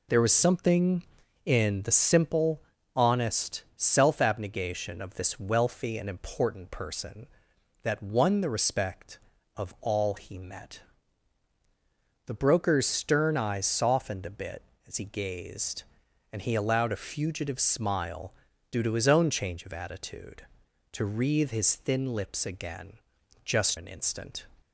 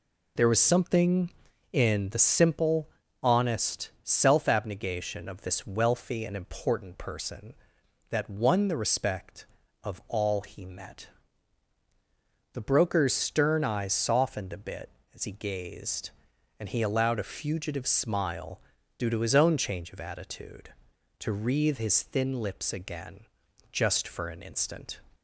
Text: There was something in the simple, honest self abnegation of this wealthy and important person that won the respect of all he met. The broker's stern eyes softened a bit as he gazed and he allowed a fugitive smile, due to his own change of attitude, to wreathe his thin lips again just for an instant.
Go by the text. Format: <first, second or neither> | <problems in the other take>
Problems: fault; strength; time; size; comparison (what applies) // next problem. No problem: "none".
second | pauses between "again" and "just"; noticeable; at 22.9 s; 0.50 s long; noticeable in the second // skips "for"; at 23.7 s